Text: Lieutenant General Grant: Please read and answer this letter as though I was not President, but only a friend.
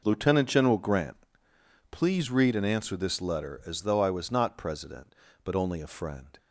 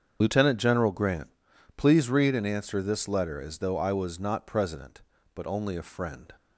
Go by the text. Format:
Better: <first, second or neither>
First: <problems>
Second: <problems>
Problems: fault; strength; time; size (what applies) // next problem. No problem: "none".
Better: first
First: none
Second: loses the start of "Lieutenant"; at 0.2 s; 35 ms // starts louder than the rest; strong; until 1.2 s; 7.5 dB